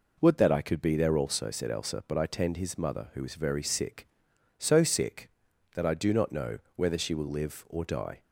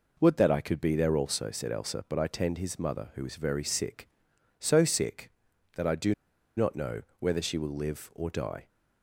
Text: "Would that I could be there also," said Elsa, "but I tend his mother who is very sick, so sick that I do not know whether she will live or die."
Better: first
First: pauses between "know" and "whether"; slight; at 6.5 s; 0.18 s long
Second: pauses between "do" and "not"; at 6.1 s; 0.43 s long // pauses between "know" and "whether"; slight; at 7.0 s; 0.18 s long

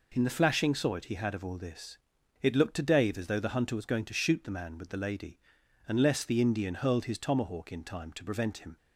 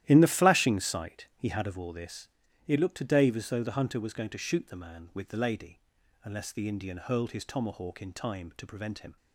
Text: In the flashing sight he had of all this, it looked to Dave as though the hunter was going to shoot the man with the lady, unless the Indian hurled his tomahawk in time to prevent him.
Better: first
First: none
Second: starts louder than the rest; strong; until 1.8 s; 13 dB

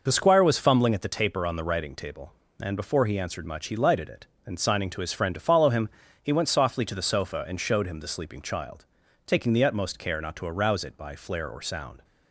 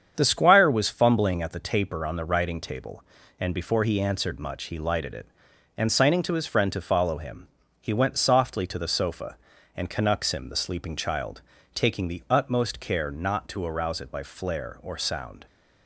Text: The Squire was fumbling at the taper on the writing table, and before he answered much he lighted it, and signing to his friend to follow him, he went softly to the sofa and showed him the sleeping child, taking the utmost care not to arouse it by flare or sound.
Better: first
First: none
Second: starts louder than the rest; strong; until 1.1 s; 7.5 dB // says "canucks" for "showed"; at 9.8 s

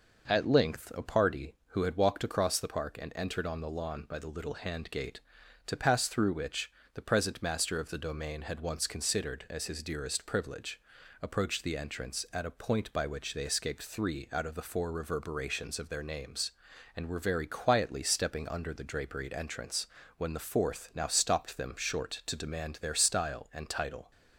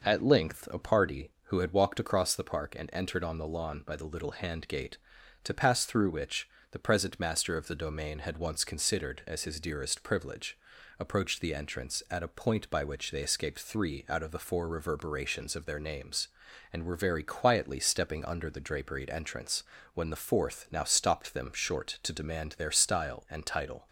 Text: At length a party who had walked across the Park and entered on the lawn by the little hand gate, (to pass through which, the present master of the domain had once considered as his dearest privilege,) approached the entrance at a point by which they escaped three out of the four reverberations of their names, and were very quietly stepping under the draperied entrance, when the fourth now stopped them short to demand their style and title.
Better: neither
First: none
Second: none

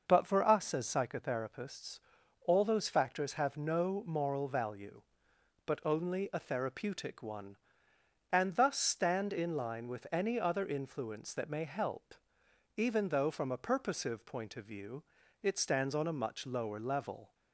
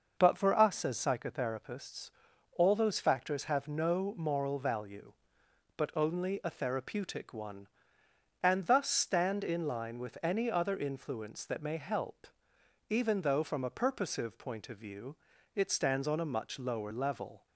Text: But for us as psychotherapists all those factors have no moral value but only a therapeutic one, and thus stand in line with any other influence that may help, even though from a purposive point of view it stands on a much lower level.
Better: neither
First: starts louder than the rest; noticeable; until 1.0 s; 6 dB // pauses between "psychotherapists" and "all"; noticeable; at 2.0 s; 0.46 s long // pauses between "view" and "it"; at 15.0 s; 0.40 s long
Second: starts louder than the rest; noticeable; until 1.1 s; 6 dB // pauses between "psychotherapists" and "all"; noticeable; at 2.1 s; 0.46 s long // pauses between "view" and "it"; at 15.1 s; 0.40 s long

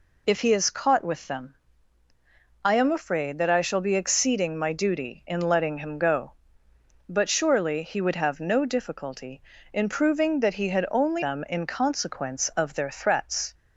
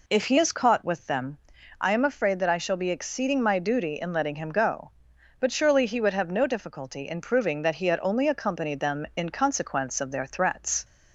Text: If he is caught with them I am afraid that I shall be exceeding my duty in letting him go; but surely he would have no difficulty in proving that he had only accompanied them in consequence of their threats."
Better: second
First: pauses between "them" and "I"; at 1.5 s; 1.0 s long // skips "accompanied"; at 11.2 s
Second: pauses between "them" and "I"; at 1.3 s; 0.42 s long

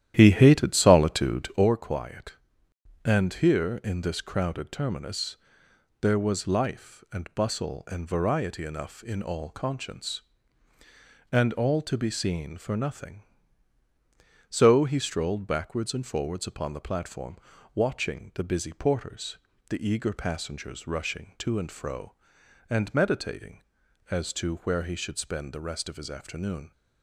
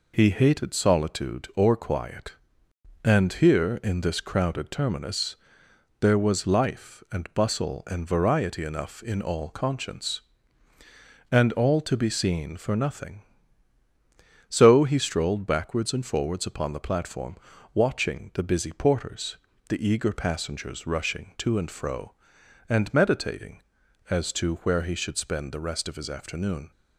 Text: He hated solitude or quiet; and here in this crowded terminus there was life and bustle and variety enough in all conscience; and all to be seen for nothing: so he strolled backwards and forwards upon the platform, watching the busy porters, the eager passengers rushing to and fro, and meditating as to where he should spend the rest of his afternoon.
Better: second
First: starts louder than the rest; strong; until 1.7 s; 11.5 dB // pauses between "terminus" and "there"; noticeable; at 5.3 s; 0.64 s long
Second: pauses between "terminus" and "there"; noticeable; at 5.3 s; 0.64 s long

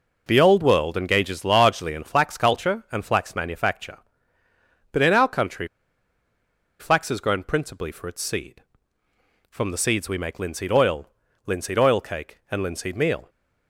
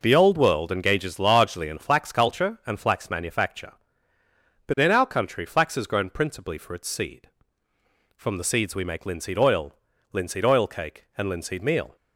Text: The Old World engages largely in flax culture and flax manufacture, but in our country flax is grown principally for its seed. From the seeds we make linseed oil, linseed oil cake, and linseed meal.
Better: second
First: pauses between "country" and "flax"; at 5.6 s; 1.1 s long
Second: none

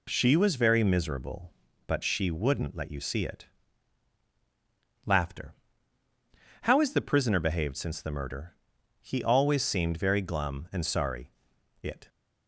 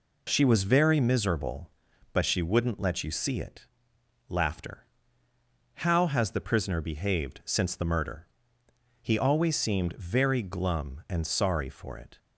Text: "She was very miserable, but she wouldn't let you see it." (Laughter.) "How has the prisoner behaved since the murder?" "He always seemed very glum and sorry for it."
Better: second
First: skips "for"; at 11.5 s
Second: none

